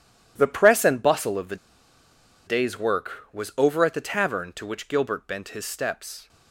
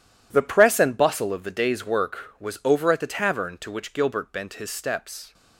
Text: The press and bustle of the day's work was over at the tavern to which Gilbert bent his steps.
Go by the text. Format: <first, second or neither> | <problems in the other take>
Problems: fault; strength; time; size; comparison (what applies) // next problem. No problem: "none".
second | pauses between "the" and "day's"; noticeable; at 1.5 s; 0.90 s long